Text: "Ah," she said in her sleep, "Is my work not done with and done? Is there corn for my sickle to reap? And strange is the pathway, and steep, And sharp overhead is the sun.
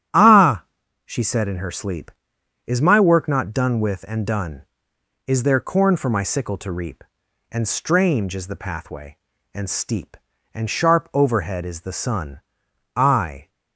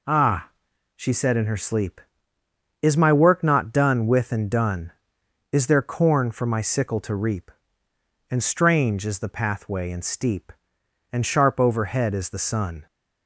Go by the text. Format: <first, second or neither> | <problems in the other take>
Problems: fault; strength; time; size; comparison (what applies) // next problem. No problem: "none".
second | starts louder than the rest; strong; until 1.5 s; 9.5 dB // goes on to say "I"; from 12.9 s on; 0.52 s long